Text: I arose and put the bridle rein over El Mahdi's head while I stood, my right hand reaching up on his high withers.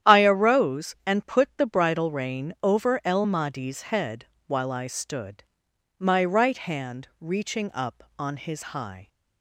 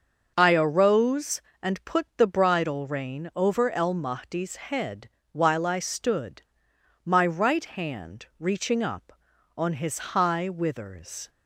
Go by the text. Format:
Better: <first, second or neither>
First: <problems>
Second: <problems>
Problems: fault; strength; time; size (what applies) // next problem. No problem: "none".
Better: second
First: starts louder than the rest; strong; until 1.1 s; 10.5 dB // pauses between "head" and "while"; slight; at 4.2 s; 0.22 s long // stops before "withers"; at 9.0 s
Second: starts louder than the rest; until 1.3 s; 6.5 dB // pauses between "head" and "while"; slight; at 5.0 s; 0.24 s long